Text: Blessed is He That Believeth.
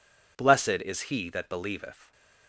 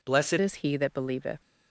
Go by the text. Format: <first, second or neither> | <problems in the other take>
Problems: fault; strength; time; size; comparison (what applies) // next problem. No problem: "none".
first | changes voice at "is"; from 0.4 s on; 1.0 s long